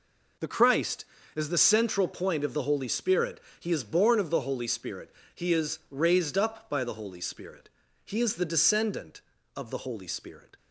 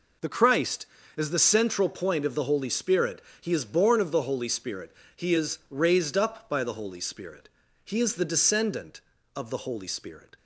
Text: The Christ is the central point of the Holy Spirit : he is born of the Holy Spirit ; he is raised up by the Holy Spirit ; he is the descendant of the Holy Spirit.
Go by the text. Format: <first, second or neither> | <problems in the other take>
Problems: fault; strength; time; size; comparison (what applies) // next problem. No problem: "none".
neither | none